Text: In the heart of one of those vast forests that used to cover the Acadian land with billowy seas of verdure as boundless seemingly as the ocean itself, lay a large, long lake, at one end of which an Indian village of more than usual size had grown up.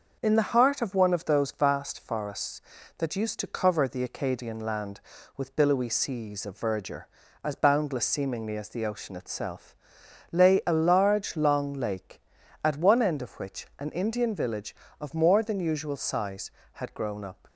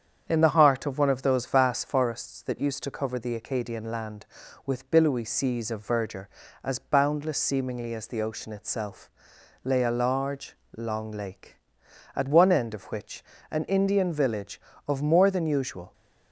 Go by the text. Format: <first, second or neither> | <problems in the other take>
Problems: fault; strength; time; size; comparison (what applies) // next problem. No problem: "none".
first | starts louder than the rest; strong; until 1.2 s; 8 dB // pauses between "which" and "an"; slight; at 13.2 s; 0.30 s long // stops before "size had grown up"; at 15.9 s